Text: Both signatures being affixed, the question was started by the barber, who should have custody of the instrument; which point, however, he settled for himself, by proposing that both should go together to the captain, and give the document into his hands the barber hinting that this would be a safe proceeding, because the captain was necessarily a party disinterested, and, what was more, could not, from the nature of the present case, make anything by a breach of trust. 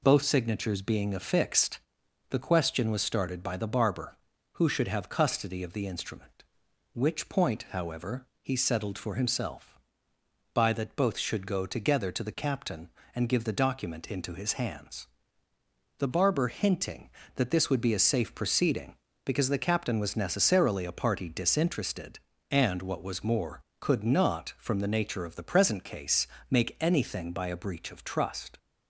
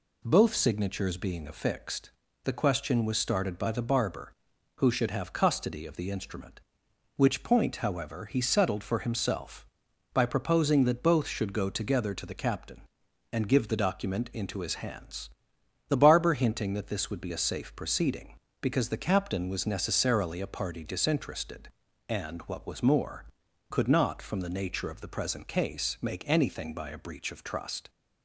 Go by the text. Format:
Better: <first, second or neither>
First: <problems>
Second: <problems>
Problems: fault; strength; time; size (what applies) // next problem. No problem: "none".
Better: second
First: skips "proposing"; at 10.7 s // pauses between "hands" and "the"; noticeable; at 15.0 s; 0.92 s long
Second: pauses between "hands" and "the"; noticeable; at 15.2 s; 0.58 s long